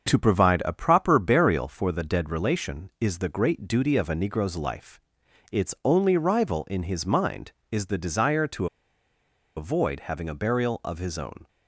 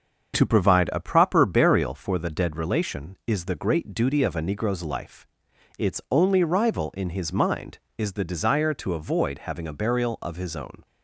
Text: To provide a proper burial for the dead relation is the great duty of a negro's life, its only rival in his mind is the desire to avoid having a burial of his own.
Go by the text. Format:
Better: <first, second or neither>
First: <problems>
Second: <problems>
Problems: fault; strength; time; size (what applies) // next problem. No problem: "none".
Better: second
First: starts louder than the rest; until 1.1 s; 6.5 dB // pauses between "to" and "avoid"; noticeable; at 8.6 s; 0.89 s long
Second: starts louder than the rest; until 1.3 s; 6.5 dB